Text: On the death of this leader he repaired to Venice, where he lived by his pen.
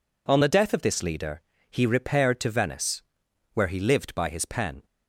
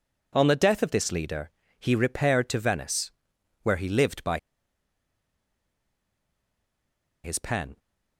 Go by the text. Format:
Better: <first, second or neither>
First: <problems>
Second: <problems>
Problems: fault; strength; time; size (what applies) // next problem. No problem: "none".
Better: first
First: pauses between "leader" and "he"; slight; at 1.4 s; 0.26 s long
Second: pauses between "leader" and "he"; slight; at 1.5 s; 0.26 s long // pauses between "by" and "his"; strong; at 4.3 s; 2.8 s long